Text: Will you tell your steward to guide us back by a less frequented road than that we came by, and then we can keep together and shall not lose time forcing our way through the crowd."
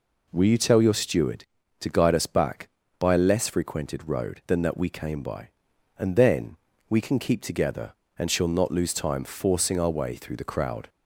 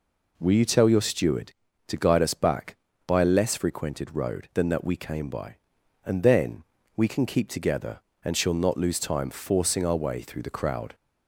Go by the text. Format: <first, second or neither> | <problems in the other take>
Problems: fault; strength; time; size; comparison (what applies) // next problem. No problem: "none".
neither | pauses between "then" and "we"; slight; the same in both